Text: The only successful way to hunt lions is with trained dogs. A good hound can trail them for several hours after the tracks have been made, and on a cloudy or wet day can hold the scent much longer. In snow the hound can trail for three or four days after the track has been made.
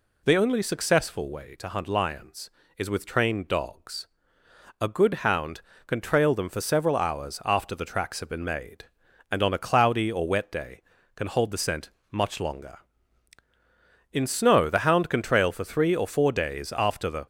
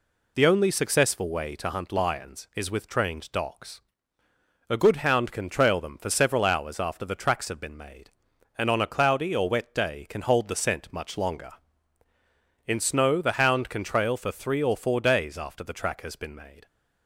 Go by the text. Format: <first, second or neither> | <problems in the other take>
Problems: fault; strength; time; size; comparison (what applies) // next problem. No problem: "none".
second | pauses between "scent" and "much"; slight; at 11.9 s; 0.20 s long // stops before "track has been made"; at 17.2 s